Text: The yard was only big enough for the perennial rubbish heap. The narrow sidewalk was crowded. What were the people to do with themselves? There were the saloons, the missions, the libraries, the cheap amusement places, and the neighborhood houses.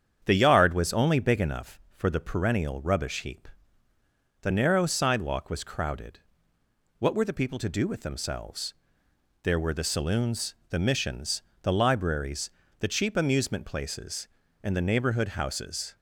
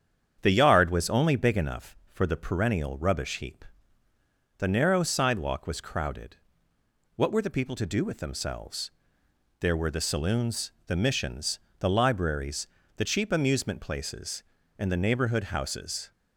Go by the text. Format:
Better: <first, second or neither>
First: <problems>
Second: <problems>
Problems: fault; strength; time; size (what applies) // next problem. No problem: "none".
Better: neither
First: starts louder than the rest; strong; until 1.2 s; 8 dB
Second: starts louder than the rest; strong; until 1.4 s; 8 dB